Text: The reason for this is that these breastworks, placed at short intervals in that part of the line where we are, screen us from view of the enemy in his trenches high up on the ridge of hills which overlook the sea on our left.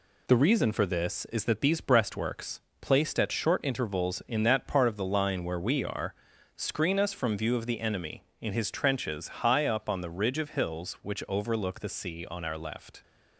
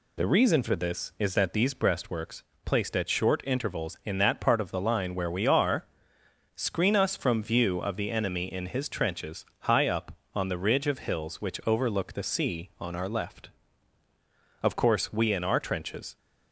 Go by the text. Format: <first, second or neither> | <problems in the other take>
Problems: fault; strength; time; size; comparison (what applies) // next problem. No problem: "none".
first | pauses between "trenches" and "high"; slight; at 9.4 s; 0.16 s long // goes on to say "Of course we in our trenches"; from 14.6 s on; 1.5 s long